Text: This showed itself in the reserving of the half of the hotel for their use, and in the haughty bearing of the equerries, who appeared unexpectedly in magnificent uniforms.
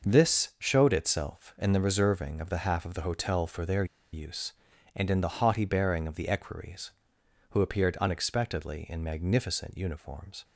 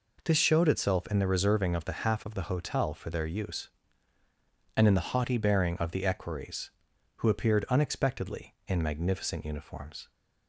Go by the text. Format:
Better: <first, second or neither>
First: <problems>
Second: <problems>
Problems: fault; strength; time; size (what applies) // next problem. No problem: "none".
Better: second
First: pauses between "their" and "use"; slight; at 3.8 s; 0.28 s long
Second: none